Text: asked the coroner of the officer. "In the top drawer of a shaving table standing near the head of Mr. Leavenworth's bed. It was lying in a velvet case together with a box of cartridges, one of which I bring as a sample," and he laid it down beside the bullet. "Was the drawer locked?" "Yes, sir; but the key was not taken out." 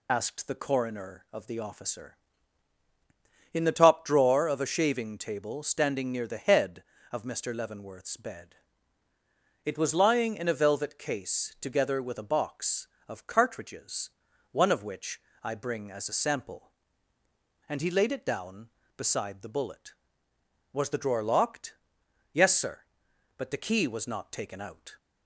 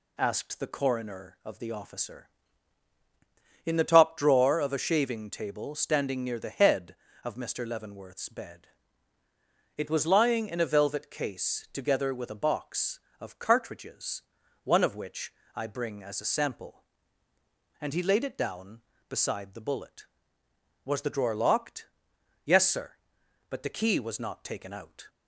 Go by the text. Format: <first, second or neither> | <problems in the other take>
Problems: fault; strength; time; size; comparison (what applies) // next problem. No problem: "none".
second | loses the start of "asked"; at 0.0 s; 30 ms // pauses between "which" and "I"; slight; at 15.2 s; 0.22 s long; slight in the second